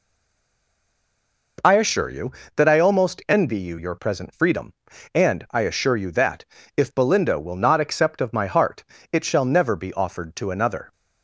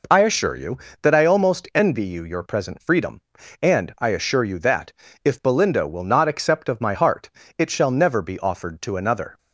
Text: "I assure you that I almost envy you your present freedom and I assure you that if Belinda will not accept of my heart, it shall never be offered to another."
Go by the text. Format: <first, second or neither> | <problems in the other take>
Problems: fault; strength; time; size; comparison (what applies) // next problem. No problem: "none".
second | stays silent before the first word; noticeable; until 1.5 s; 1.5 s long // pauses between "that" and "if"; slight; at 6.4 s; 0.32 s long; slight in the second